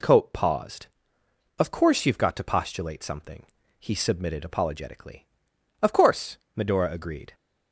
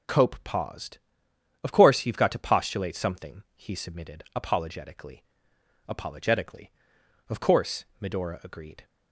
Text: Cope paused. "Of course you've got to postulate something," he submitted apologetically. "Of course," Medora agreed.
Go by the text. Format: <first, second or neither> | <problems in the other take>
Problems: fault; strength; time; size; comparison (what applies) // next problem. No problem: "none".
first | says "apologetically" twice; at 5.8 s